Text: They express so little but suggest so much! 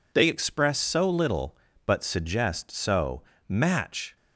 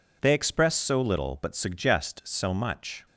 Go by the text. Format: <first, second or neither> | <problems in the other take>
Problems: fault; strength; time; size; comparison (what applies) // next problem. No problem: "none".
second | says "match" for "much"; at 3.4 s